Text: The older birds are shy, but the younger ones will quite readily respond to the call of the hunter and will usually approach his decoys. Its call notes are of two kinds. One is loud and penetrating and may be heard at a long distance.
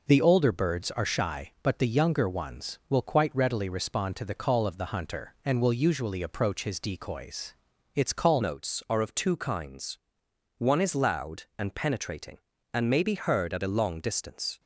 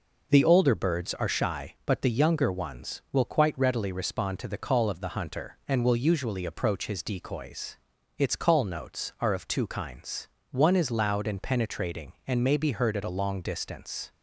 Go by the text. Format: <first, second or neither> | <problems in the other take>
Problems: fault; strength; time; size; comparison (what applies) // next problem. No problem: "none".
second | changes voice at "notes"; from 8.4 s on; 6.1 s long